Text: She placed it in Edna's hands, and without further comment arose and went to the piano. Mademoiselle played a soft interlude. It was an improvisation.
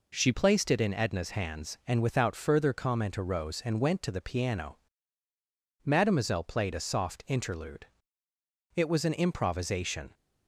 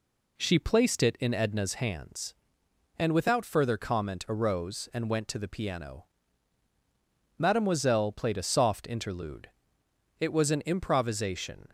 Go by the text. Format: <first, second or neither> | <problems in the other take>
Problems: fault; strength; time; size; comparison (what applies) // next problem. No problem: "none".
second | changes voice at "placed"; from 0.3 s on; 9.8 s long